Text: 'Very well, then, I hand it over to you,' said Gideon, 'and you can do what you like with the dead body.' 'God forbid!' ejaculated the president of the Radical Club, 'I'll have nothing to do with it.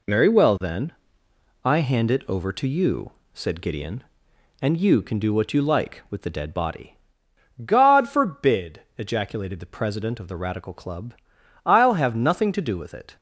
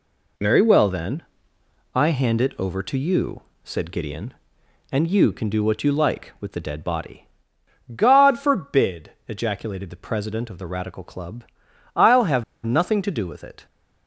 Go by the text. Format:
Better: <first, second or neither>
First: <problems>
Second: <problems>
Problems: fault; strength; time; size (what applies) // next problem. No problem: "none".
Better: first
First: none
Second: pauses between "have" and "nothing"; slight; at 12.4 s; 0.19 s long